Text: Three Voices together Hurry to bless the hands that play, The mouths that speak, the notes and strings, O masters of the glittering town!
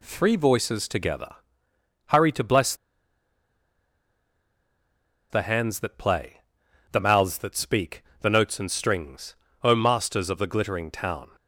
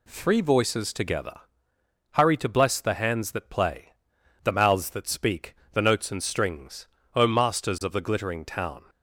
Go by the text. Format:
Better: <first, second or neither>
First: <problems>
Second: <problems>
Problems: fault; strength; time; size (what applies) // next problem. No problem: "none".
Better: second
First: pauses between "together" and "Hurry"; noticeable; at 1.3 s; 0.70 s long // pauses between "bless" and "the"; strong; at 2.7 s; 2.5 s long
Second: pauses between "together" and "Hurry"; noticeable; at 1.4 s; 0.70 s long